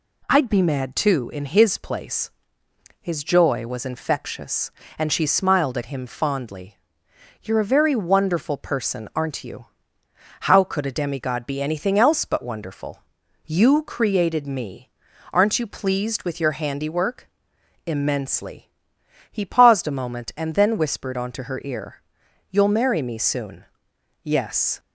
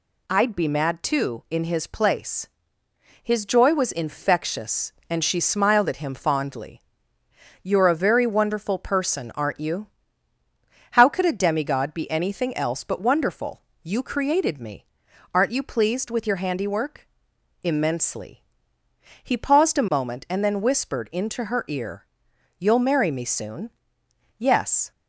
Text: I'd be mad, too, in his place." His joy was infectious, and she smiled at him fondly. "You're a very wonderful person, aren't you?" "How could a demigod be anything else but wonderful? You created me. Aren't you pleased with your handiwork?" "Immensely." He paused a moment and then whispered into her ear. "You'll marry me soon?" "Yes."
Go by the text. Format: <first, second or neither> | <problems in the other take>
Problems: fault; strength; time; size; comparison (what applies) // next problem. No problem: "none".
second | says "onto" for "into"; at 21.1 s